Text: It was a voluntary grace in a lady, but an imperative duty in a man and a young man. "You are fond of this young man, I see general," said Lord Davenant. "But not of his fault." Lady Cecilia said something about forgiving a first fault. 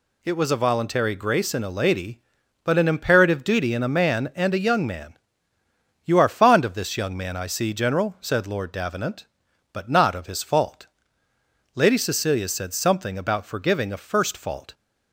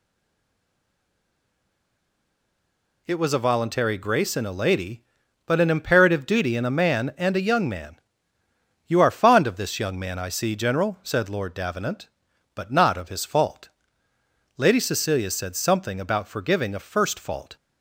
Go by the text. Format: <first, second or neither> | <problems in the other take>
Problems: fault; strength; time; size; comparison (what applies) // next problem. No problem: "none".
first | stays silent before the first word; strong; until 3.0 s; 3.0 s long